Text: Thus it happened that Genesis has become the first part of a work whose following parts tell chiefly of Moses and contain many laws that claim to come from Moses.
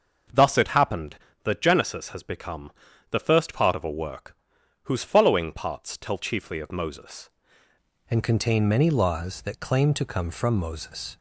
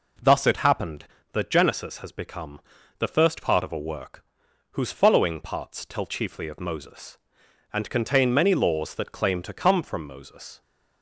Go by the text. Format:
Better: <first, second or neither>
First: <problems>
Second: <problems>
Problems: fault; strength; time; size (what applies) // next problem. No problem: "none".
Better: second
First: starts louder than the rest; until 1.5 s; 6.5 dB // pauses between "become" and "the"; at 2.7 s; 0.40 s long // pauses between "work" and "whose"; noticeable; at 4.3 s; 0.48 s long // changes voice at "and"; from 8.1 s on; 3.0 s long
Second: pauses between "become" and "the"; at 2.5 s; 0.39 s long // pauses between "work" and "whose"; noticeable; at 4.2 s; 0.48 s long